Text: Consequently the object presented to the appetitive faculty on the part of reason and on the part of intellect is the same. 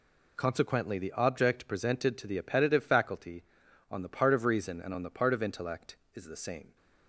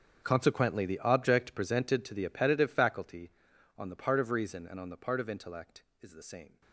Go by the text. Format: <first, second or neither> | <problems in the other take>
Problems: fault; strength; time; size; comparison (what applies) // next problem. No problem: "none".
first | gets quieter; strong; throughout; 18.5 dB